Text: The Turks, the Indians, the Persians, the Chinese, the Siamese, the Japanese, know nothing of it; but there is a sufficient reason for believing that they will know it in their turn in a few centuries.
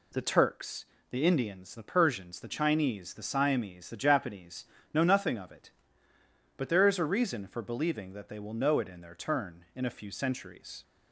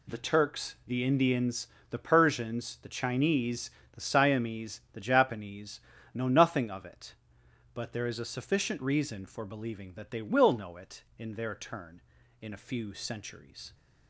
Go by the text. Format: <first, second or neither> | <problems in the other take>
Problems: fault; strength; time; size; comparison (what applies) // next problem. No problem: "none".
second | skips "sufficient"; at 7.1 s